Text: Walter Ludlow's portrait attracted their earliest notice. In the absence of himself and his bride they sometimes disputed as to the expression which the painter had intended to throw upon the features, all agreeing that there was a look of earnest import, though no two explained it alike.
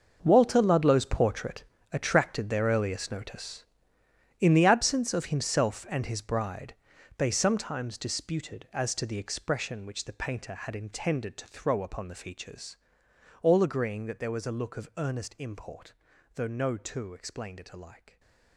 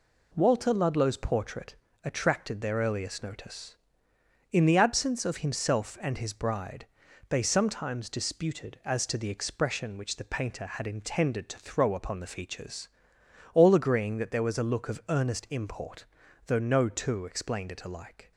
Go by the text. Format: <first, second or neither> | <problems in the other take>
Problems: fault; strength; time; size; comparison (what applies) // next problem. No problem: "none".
second | gets quieter; strong; throughout; 14.5 dB // pauses between "portrait" and "attracted"; slight; at 1.6 s; 0.30 s long; slight in the second // pauses between "bride" and "they"; at 6.7 s; 0.42 s long; also in the second